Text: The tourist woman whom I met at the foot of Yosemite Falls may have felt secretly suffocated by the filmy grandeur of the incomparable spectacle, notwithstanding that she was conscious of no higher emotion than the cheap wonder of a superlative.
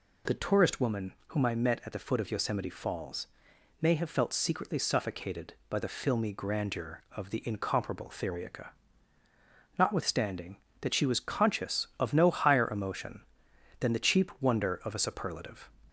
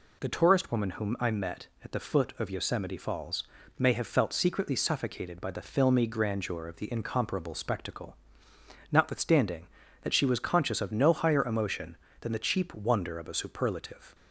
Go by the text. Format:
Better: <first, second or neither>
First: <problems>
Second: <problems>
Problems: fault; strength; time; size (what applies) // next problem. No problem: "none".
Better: second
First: pauses between "woman" and "whom"; slight; at 1.1 s; 0.16 s long // pauses between "Falls" and "may"; noticeable; at 3.2 s; 0.52 s long // says "theriaca" for "spectacle"; at 8.0 s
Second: pauses between "Falls" and "may"; slight; at 3.4 s; 0.34 s long